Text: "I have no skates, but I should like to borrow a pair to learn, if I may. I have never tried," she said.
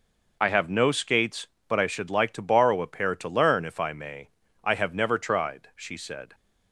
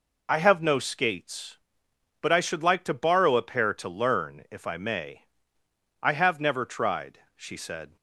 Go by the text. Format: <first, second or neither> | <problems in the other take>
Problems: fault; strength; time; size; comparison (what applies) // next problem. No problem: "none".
neither | none